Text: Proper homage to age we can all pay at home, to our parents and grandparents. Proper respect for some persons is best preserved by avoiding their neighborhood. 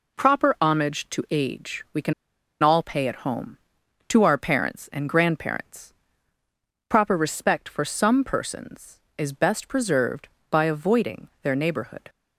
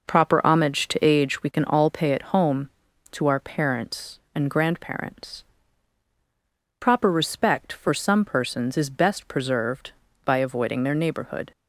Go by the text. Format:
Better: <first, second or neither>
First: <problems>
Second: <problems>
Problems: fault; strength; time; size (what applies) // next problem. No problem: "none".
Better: second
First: pauses between "can" and "all"; noticeable; at 2.1 s; 0.49 s long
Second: none